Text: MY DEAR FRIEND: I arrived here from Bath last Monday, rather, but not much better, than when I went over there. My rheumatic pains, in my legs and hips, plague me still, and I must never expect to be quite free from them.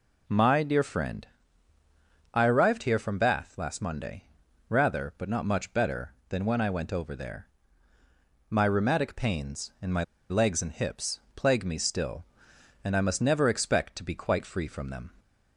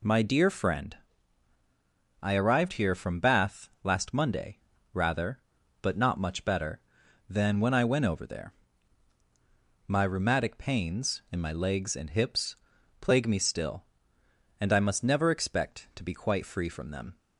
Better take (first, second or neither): second